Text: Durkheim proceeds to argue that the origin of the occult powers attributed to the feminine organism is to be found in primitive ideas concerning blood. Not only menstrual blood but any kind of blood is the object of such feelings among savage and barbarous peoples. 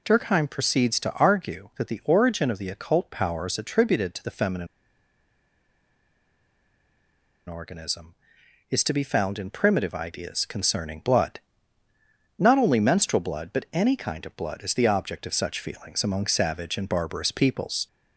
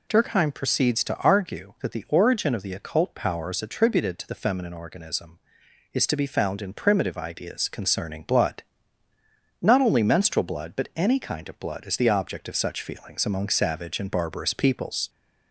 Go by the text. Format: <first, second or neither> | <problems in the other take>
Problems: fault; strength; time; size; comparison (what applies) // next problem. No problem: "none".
second | pauses between "feminine" and "organism"; strong; at 4.6 s; 2.8 s long